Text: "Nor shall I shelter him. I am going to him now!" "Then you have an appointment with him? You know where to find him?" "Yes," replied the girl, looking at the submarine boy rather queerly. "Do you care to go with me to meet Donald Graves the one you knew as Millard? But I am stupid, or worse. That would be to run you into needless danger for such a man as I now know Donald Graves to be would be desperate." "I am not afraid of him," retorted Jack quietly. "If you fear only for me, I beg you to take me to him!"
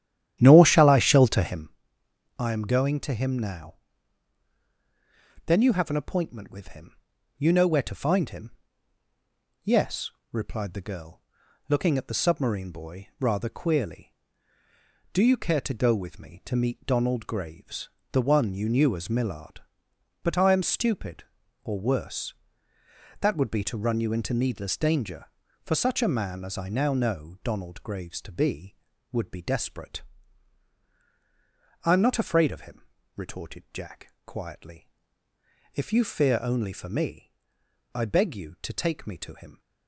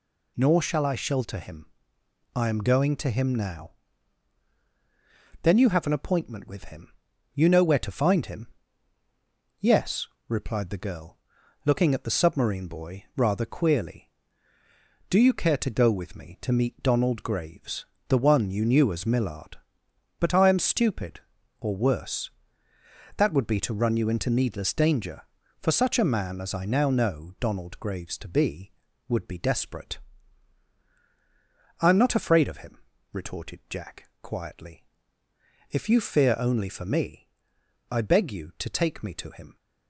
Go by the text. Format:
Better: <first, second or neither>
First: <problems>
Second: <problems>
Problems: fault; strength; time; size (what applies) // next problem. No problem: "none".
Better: second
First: starts louder than the rest; strong; until 1.8 s; 11 dB // pauses between "Graves" and "the"; slight; at 17.8 s; 0.24 s long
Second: pauses between "Graves" and "the"; slight; at 17.8 s; 0.24 s long